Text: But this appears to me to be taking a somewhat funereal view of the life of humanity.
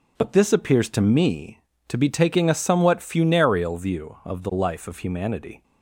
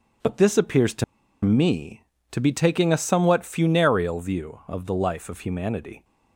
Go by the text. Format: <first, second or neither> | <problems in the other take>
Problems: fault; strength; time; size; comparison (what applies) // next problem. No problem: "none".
first | starts louder than the rest; until 1.6 s; 6 dB; also in the first // pauses between "to" and "me"; at 1.0 s; 0.40 s long